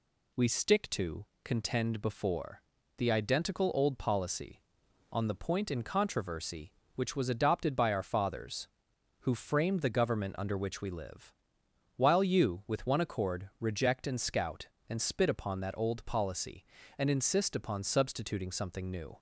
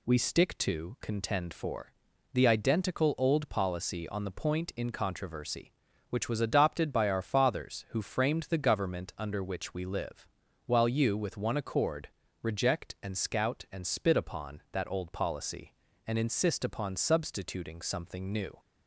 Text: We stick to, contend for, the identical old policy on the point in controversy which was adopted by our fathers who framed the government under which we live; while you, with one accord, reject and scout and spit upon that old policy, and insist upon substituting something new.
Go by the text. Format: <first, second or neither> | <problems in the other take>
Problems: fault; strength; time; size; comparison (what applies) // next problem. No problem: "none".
second | says "before" for "for"; at 2.0 s